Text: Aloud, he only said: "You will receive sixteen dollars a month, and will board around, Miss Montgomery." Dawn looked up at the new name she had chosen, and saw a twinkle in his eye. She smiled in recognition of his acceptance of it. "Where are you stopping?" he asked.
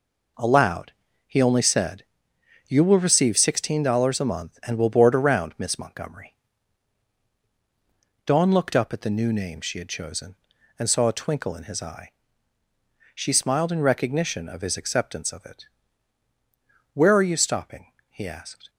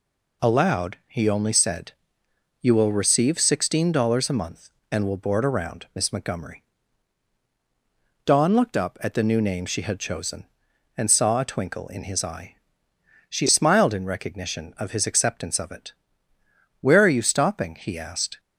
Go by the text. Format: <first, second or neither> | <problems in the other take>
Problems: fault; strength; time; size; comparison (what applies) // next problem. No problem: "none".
neither | none